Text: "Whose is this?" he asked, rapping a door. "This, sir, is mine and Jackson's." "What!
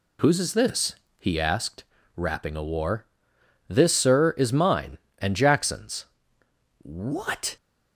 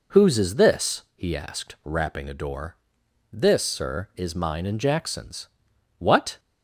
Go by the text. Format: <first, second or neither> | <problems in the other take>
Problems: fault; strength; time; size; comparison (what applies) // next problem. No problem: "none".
second | says "war" for "door"; at 2.6 s